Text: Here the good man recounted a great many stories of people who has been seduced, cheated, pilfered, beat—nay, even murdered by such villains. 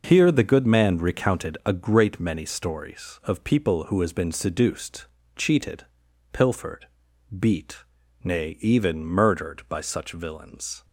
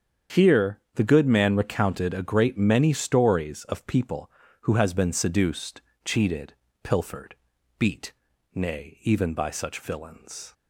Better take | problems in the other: first | starts louder than the rest; strong; until 1.4 s; 8 dB // pauses between "Here" and "the"; slight; at 0.7 s; 0.16 s long // skips "murdered"; at 9.3 s

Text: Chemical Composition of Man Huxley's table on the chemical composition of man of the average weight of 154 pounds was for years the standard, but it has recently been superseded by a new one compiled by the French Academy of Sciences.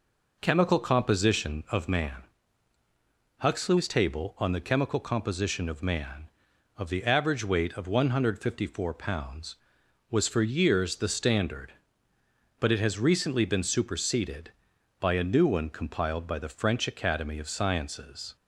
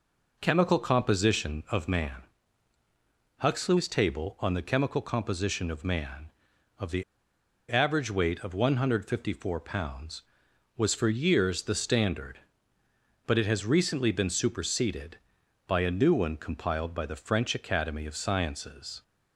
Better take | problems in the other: first | pauses between "Man" and "Huxley's"; at 2.2 s; 1.1 s long; also in the first // pauses between "the" and "average"; noticeable; at 7.0 s; 0.66 s long

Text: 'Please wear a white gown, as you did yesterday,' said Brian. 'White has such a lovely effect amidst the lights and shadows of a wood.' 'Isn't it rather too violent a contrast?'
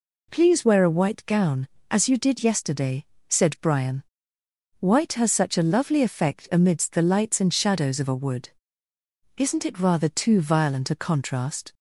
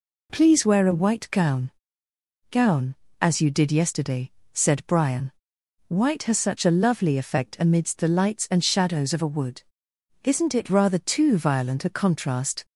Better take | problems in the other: first | says "gown" twice; at 2.5 s

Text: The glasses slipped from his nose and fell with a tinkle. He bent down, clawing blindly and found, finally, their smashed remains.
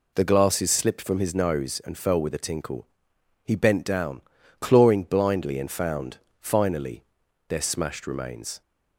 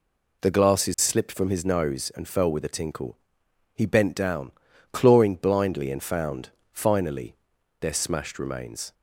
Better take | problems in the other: neither | none

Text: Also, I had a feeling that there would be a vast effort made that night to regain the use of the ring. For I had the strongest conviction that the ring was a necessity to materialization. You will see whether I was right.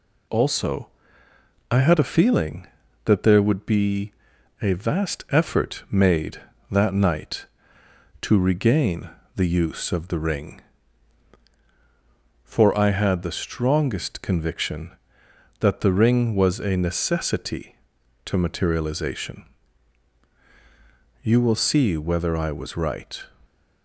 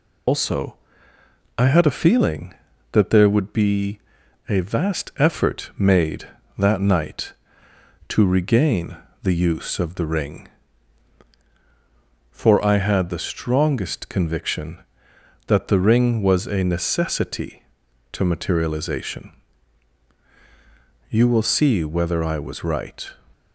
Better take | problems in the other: first | loses the start of "Also"; at 0.2 s; 120 ms // pauses between "be" and "a"; noticeable; at 3.9 s; 0.48 s long; noticeable in the first // pauses between "regain" and "the"; slight; at 8.9 s; 0.28 s long; slight in the first

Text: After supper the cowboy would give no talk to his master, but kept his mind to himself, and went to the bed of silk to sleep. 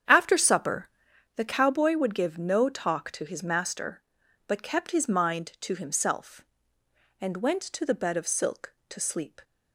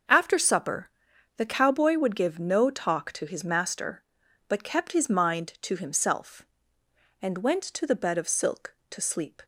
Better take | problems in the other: second | starts louder than the rest; strong; until 1.2 s; 8.5 dB // pauses between "supper" and "the"; noticeable; at 0.8 s; 0.46 s long; noticeable in the second

